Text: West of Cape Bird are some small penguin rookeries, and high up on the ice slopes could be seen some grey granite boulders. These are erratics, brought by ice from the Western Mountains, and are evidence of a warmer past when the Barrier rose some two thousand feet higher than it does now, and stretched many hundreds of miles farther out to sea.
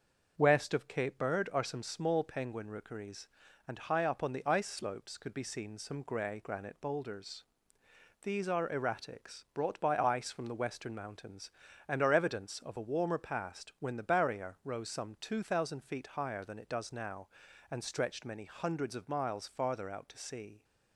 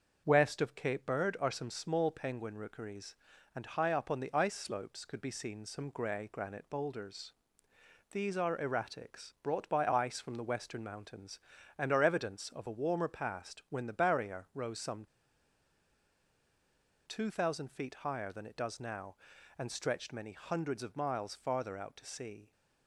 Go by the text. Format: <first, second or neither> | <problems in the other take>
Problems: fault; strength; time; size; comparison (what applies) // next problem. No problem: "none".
first | starts louder than the rest; until 1.2 s; 6 dB; also in the first // pauses between "some" and "two"; strong; at 15.0 s; 1.9 s long